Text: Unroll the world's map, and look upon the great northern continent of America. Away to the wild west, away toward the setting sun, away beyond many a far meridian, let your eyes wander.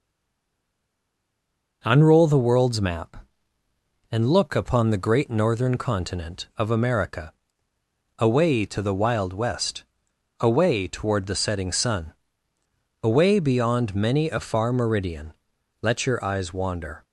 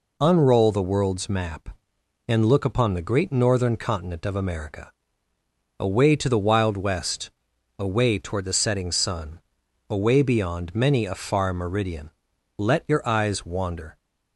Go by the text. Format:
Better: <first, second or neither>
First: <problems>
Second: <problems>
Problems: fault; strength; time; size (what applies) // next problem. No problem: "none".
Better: second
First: stays silent before the first word; noticeable; until 1.8 s; 1.8 s long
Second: none